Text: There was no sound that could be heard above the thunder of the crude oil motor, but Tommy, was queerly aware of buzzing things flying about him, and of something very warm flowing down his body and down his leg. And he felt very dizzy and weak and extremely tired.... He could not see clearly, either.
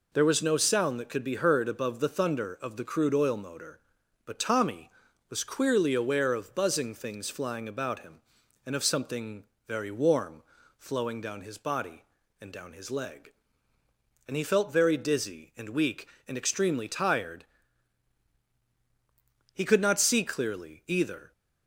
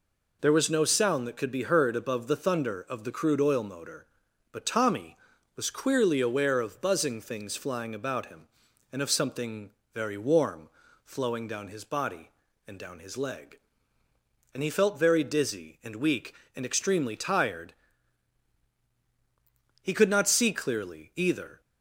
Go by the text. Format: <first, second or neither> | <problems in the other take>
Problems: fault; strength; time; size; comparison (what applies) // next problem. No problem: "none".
neither | pauses between "something" and "very"; slight; the same in both // pauses between "warm" and "flowing"; slight; the same in both